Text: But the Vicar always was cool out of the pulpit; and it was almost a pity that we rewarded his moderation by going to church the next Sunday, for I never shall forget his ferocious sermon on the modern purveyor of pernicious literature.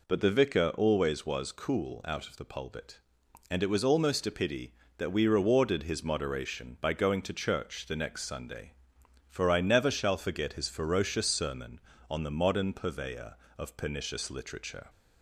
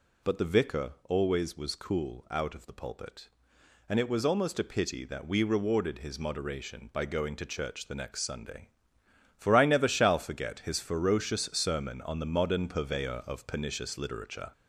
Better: first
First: none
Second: gets louder; throughout; 3.5 dB

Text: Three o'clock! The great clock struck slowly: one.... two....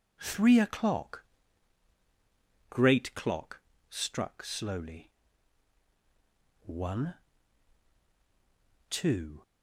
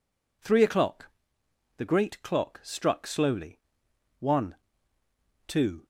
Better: second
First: skips "The"; at 1.9 s // pauses between "clock" and "struck"; slight; at 3.5 s; 0.28 s long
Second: none

